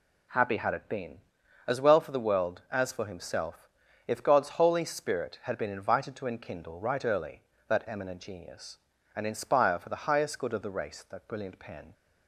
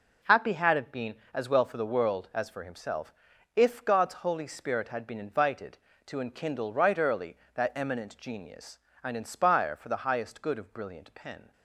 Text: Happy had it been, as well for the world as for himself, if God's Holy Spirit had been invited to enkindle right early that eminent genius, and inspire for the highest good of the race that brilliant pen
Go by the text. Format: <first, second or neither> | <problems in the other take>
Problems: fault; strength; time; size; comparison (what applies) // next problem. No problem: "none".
first | skips "the race that"; at 10.7 s